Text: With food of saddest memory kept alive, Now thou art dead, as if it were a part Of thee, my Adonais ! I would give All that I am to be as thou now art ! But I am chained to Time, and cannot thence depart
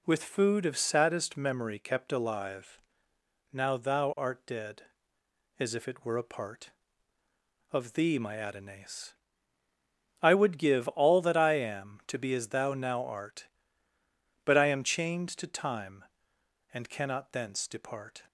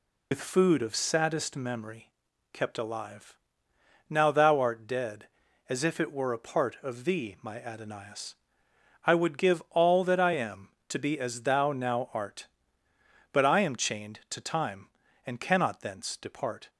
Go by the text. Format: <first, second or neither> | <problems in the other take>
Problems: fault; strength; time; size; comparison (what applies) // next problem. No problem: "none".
first | loses the start of "With"; at 0.3 s; 80 ms // pauses between "memory" and "kept"; noticeable; at 2.0 s; 0.46 s long